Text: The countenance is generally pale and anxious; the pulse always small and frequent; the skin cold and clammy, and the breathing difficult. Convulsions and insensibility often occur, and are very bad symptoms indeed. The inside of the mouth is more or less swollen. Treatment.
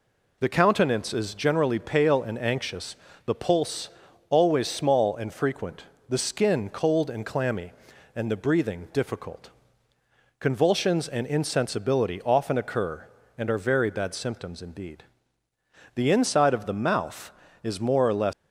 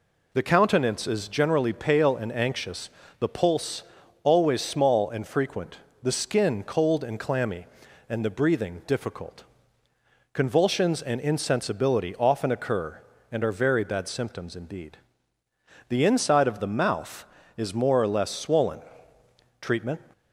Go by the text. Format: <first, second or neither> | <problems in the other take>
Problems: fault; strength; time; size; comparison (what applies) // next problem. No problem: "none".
second | pauses between "pulse" and "always"; at 3.8 s; 0.40 s long; also in the second // stops before "swollen Treatment"; at 18.3 s